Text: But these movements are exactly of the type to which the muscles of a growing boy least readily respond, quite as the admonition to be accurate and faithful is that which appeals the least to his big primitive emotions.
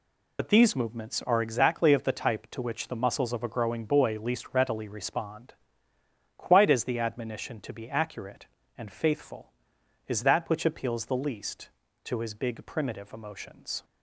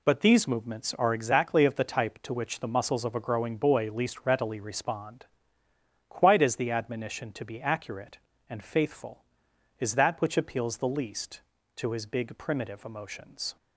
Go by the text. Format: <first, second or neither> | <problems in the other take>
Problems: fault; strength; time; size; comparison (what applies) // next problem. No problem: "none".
second | loses the start of "But"; at 0.3 s; 70 ms